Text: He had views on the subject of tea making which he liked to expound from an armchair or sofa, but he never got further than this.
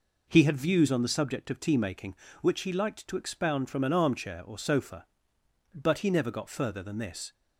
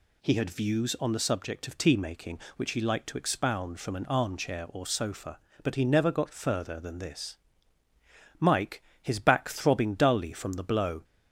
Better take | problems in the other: first | goes on to say "Mike his back throbbing dully from the blow"; strong; from 8.3 s on; 2.6 s long

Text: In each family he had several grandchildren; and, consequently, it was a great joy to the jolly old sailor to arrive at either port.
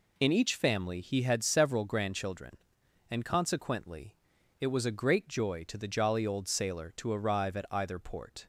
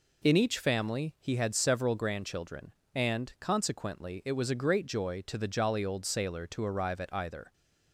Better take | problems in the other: first | stops before "port"; at 7.5 s

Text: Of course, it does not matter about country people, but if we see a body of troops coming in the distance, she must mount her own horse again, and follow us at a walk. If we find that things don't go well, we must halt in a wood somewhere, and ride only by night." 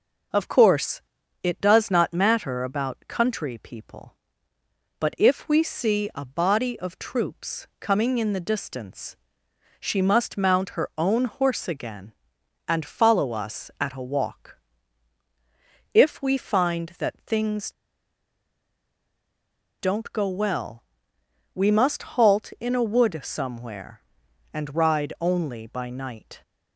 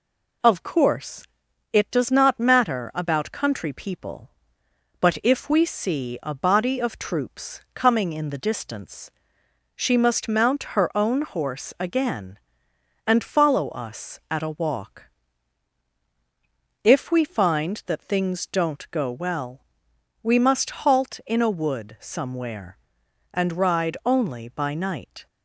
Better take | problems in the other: second | pauses between "things" and "don't"; strong; at 17.7 s; 2.0 s long

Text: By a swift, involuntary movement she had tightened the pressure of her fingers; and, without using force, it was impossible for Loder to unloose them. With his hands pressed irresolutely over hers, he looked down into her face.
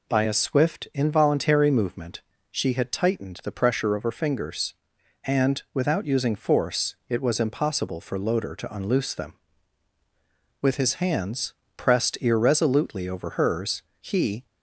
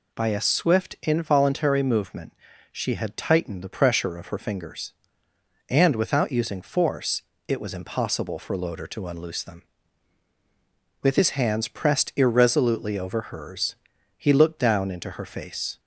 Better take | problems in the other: second | pauses between "movement" and "she"; slight; at 2.2 s; 0.30 s long; also in the second // pauses between "hands" and "pressed"; slight; at 11.5 s; 0.22 s long // stops before "looked down into her face"; at 14.4 s

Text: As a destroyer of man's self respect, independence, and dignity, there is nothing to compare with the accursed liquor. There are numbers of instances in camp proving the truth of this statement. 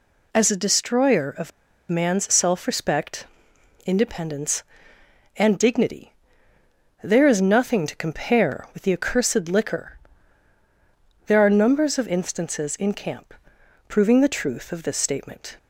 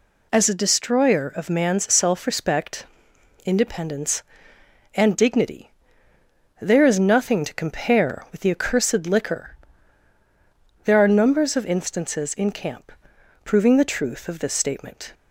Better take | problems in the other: second | pauses between "of" and "man's"; at 1.5 s; 0.38 s long // pauses between "camp" and "proving"; noticeable; at 13.3 s; 0.54 s long; noticeable in the second

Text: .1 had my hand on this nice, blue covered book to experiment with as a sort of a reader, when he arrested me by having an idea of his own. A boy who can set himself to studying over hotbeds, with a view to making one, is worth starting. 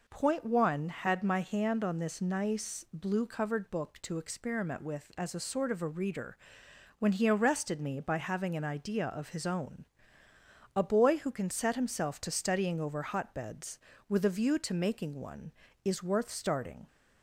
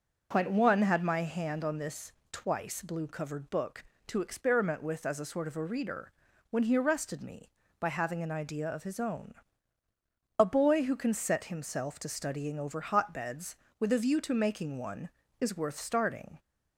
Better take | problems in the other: first | says "twice" for "nice"; at 2.3 s

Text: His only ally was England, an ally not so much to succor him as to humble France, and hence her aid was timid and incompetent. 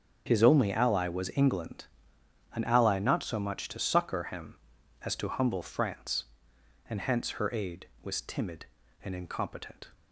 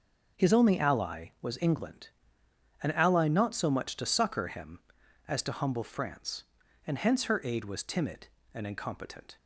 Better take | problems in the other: neither | starts louder than the rest; the same in both

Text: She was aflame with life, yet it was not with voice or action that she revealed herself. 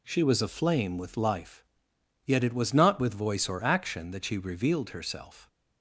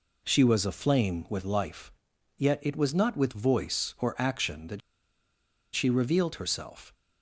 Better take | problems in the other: first | pauses between "that" and "she"; noticeable; at 4.8 s; 0.92 s long

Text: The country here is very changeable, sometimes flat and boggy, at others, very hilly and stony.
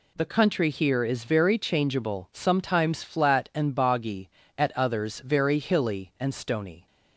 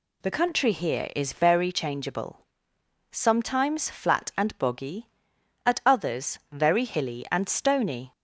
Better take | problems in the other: first | changes voice at "country"; from 0.3 s on; 7.8 s long

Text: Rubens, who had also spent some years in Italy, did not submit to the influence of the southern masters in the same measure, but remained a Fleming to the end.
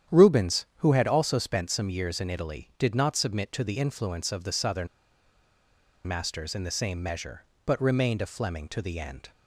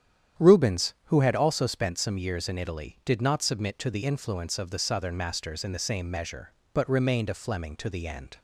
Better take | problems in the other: second | starts louder than the rest; strong; until 1.2 s; 9.5 dB; strong in the second // pauses between "southern" and "masters"; at 4.8 s; 1.1 s long

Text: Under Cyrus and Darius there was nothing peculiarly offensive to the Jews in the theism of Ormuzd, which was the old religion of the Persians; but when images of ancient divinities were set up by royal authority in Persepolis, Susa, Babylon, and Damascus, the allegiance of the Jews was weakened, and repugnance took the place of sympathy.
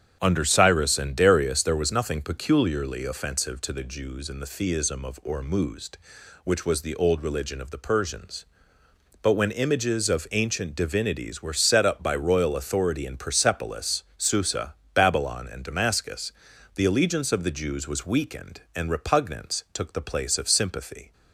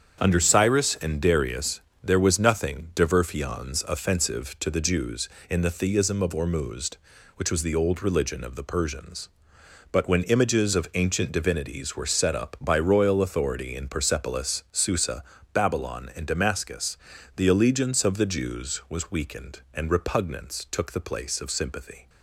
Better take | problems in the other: first | starts louder than the rest; strong; until 1.2 s; 7.5 dB; strong in the first // pauses between "Darius" and "there"; slight; at 1.7 s; 0.24 s long // says "diverfions" for "peculiarly"; at 2.9 s

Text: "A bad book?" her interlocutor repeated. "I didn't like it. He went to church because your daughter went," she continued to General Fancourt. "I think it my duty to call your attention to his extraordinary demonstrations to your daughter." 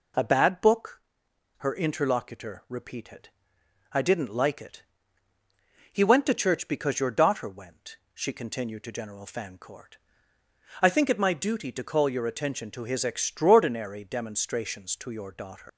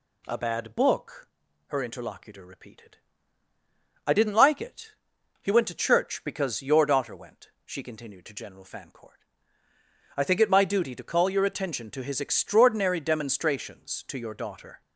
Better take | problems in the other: second | leaves "daughter" unfinished; at 15.6 s; 115 ms

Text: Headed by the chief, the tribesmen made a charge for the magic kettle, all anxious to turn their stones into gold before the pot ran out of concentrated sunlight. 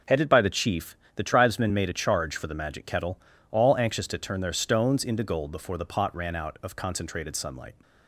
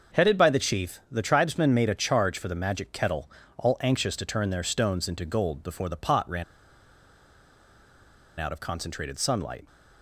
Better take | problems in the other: first | starts louder than the rest; until 1.2 s; 6 dB // pauses between "ran" and "out"; strong; at 6.4 s; 1.9 s long

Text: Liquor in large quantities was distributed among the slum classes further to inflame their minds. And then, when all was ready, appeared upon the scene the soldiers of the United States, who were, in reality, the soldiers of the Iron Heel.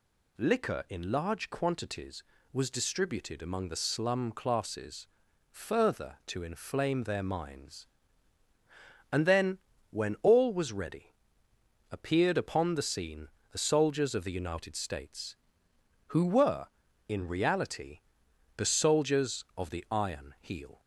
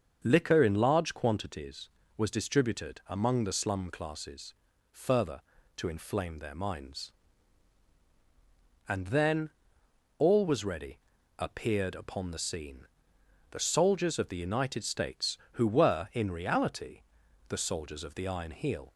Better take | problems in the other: first | starts louder than the rest; until 1.2 s; 6.5 dB // pauses between "classes" and "further"; at 4.5 s; 0.38 s long; noticeable in the first // skips "when"; at 9.8 s // pauses between "scene" and "the"; noticeable; at 12.8 s; 0.64 s long; slight in the first

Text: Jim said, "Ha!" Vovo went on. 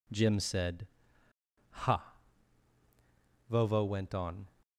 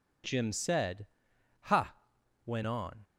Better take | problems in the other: first | skips "Vovo"; at 2.1 s

